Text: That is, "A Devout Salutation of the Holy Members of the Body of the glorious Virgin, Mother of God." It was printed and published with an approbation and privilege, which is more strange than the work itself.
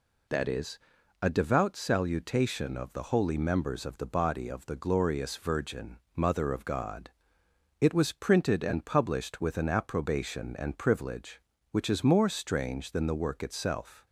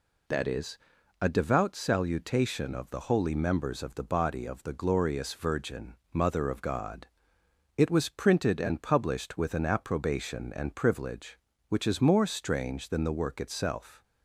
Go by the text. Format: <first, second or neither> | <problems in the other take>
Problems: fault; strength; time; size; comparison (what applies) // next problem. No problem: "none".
neither | none